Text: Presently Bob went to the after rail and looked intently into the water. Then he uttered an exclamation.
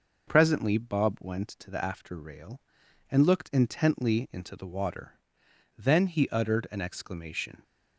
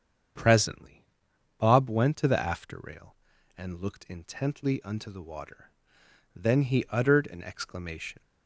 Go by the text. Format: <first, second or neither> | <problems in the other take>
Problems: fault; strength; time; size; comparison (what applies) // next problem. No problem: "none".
first | starts louder than the rest; strong; until 1.8 s; 7.5 dB // pauses between "Presently" and "Bob"; noticeable; at 1.0 s; 0.50 s long // says "unto" for "into"; at 4.8 s